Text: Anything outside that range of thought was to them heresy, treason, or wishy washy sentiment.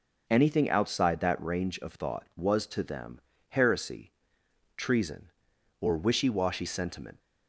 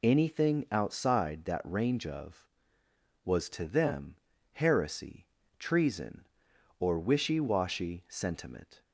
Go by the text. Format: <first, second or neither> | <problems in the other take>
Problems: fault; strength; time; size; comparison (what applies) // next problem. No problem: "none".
first | skips "thought"; at 2.8 s // pauses between "them" and "heresy"; slight; at 4.1 s; 0.36 s long; slight in the first